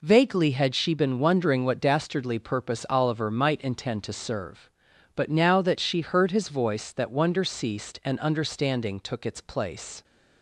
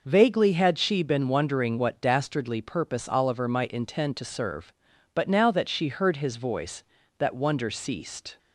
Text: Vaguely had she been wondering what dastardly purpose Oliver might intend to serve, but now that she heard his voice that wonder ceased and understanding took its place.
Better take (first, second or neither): first